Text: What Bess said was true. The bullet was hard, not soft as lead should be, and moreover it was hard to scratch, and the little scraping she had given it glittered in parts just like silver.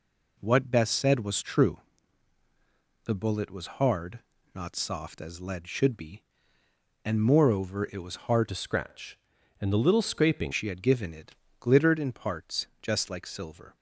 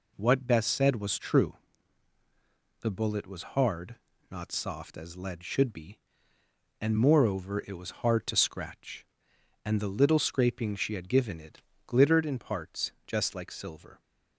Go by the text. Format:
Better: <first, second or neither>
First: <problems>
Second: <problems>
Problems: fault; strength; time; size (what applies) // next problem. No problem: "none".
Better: second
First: changes voice from "to" to "scraping"; from 8.4 to 10.5 s; 2.1 s long // pauses between "it" and "glittered"; slight; at 11.3 s; 0.24 s long // pauses between "parts" and "just"; slight; at 12.6 s; 0.16 s long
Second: pauses between "it" and "glittered"; slight; at 11.6 s; 0.24 s long // pauses between "parts" and "just"; slight; at 12.9 s; 0.16 s long